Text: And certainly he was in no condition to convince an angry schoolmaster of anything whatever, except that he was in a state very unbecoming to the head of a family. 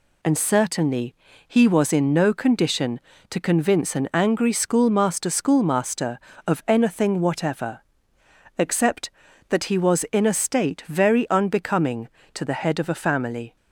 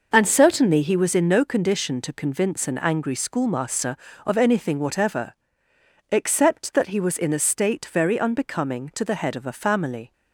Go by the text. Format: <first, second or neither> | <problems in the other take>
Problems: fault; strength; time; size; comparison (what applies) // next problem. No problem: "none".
second | pauses between "certainly" and "he"; slight; at 1.1 s; 0.32 s long // says "schoolmaster" twice; at 5.2 s